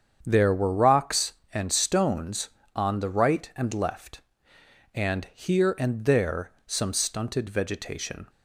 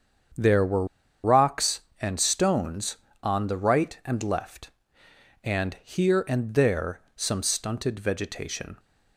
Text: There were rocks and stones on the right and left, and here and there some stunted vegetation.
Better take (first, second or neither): first